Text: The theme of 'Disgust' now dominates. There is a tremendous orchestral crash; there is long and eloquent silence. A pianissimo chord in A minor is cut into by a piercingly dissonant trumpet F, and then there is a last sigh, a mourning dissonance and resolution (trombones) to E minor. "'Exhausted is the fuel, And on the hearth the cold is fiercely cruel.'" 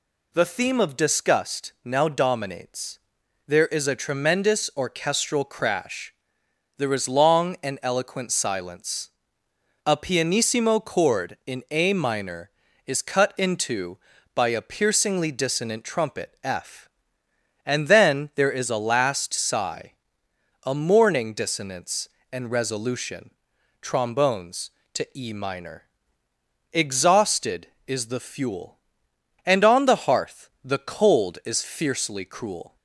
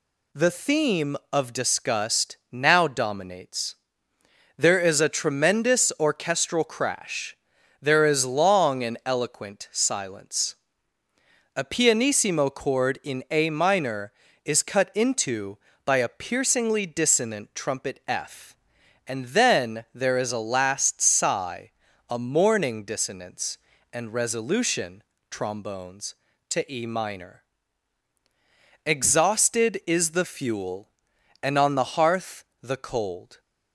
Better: first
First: none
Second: pauses between "Disgust" and "now"; slight; at 2.3 s; 0.16 s long // pauses between "hearth" and "the"; slight; at 32.4 s; 0.16 s long // stops before "is fiercely cruel"; at 33.3 s

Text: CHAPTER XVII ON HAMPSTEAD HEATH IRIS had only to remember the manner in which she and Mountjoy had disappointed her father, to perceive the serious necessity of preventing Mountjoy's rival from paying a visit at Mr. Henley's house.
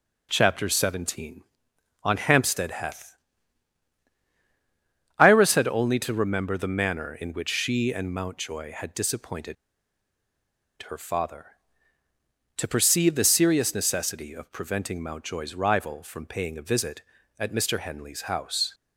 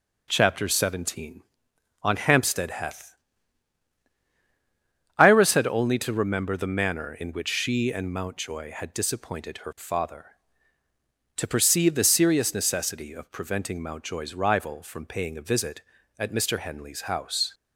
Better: second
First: pauses between "HEATH" and "IRIS"; strong; at 3.1 s; 2.0 s long // pauses between "disappointed" and "her"; strong; at 9.5 s; 1.3 s long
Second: pauses between "HEATH" and "IRIS"; strong; at 3.1 s; 2.0 s long

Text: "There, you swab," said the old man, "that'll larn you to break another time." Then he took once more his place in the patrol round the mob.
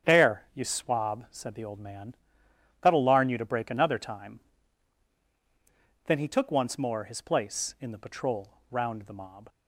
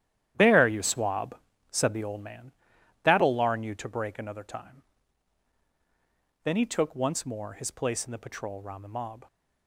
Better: first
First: starts louder than the rest; strong; until 1.1 s; 8.5 dB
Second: gets quieter; strong; throughout; 11 dB // starts louder than the rest; strong; until 1.3 s; 11 dB

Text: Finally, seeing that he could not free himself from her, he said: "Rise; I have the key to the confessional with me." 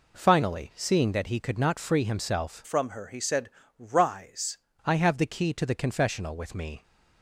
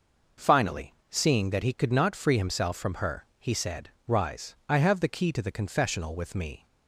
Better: second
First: changes voice from "from" to "Rise"; from 2.6 to 4.5 s; 1.9 s long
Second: none

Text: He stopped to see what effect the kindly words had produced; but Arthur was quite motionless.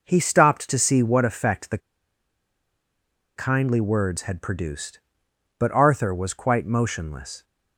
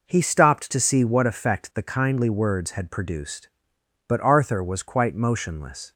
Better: second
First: pauses between "the" and "kindly"; strong; at 1.7 s; 1.5 s long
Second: none

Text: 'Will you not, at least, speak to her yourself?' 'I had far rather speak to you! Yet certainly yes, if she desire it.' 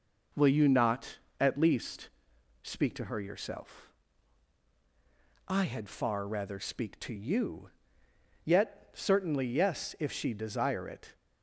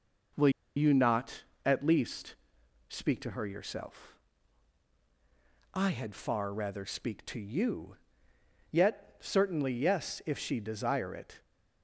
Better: first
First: none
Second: pauses between "Will" and "you"; slight; at 0.4 s; 0.27 s long

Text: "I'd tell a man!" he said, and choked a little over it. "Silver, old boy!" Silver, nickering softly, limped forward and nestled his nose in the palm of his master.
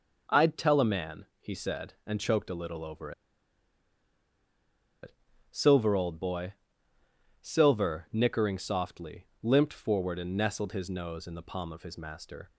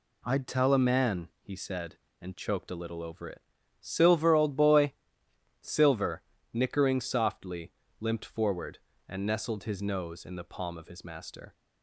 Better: second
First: pauses between "over" and "it"; strong; at 3.1 s; 1.9 s long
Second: none

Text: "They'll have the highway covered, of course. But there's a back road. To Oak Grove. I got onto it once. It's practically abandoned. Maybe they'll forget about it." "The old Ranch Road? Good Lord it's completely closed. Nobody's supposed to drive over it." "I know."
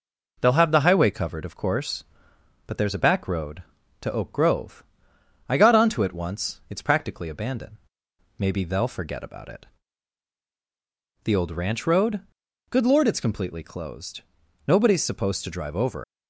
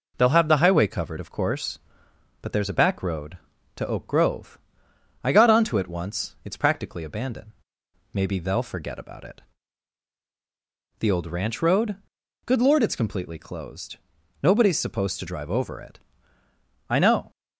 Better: second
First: stops before "it I know"; at 16.0 s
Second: none

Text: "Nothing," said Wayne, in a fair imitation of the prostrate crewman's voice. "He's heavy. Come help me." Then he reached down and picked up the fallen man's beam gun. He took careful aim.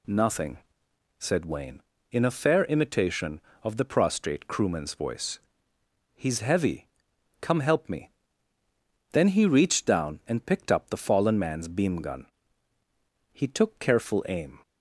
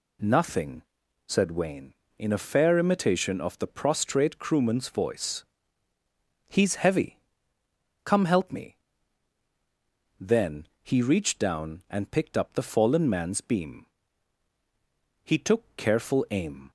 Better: first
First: none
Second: pauses between "Then" and "he"; slight; at 10.6 s; 0.16 s long // skips "gun"; at 14.5 s

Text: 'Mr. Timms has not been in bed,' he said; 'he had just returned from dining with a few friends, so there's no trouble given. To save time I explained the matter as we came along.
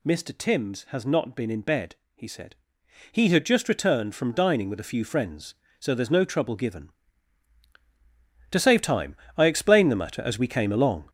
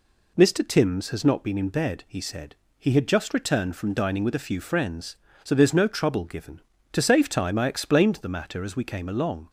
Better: second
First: gets louder; throughout; 6.5 dB // pauses between "time" and "I"; slight; at 9.1 s; 0.22 s long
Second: none

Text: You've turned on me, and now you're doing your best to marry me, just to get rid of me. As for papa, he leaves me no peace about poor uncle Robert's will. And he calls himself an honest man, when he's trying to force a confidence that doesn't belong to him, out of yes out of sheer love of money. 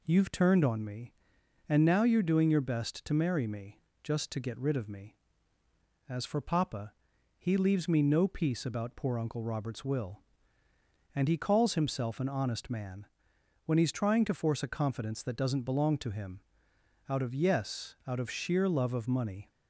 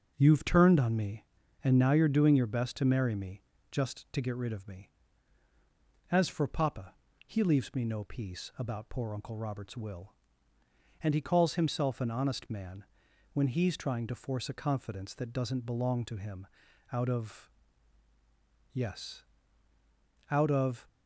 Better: first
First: none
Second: starts louder than the rest; until 1.1 s; 6.5 dB // pauses between "of" and "yes"; at 17.4 s; 1.2 s long // pauses between "yes" and "out"; at 19.2 s; 1.0 s long // stops before "sheer love of money"; at 20.8 s

